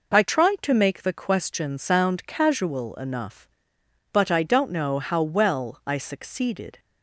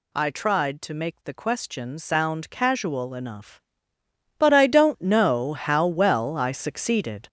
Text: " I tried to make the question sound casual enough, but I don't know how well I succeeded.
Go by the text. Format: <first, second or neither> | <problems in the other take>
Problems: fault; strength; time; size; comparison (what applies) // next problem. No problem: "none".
first | gets louder; strong; throughout; 7.5 dB